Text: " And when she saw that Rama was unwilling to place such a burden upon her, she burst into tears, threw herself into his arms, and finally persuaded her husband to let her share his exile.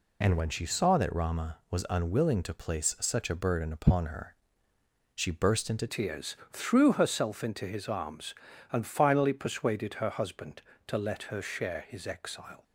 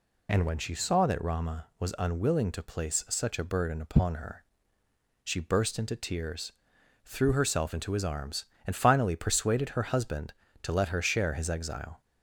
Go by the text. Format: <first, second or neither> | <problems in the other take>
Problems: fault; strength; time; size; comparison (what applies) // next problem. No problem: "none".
second | changes voice at "tears"; from 5.8 s on; 6.8 s long